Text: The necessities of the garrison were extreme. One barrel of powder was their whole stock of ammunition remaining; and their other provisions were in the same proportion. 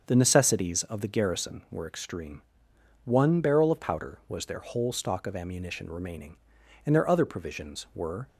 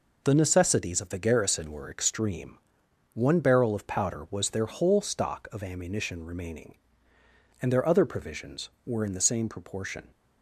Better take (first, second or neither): second